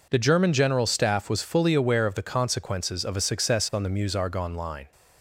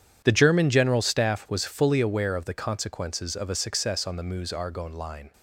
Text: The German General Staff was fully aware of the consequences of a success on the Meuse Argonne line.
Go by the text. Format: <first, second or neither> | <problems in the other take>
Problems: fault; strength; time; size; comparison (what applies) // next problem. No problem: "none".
first | gets quieter; strong; throughout; 15 dB